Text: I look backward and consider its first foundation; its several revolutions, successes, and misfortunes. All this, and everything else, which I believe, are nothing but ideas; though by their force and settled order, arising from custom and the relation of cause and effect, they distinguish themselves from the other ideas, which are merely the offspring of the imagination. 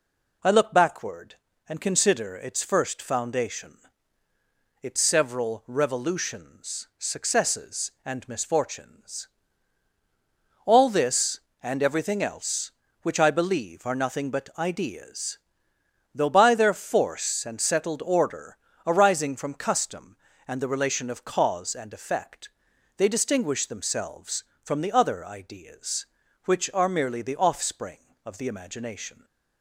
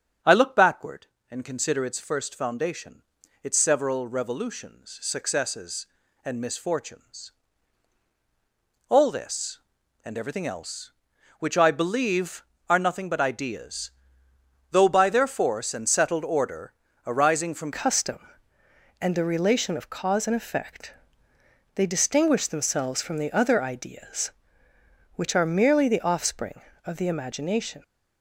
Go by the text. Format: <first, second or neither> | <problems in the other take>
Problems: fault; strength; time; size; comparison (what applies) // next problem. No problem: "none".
first | starts louder than the rest; strong; until 1.4 s; 7.5 dB // changes voice at "custom"; from 17.7 s on; 10.1 s long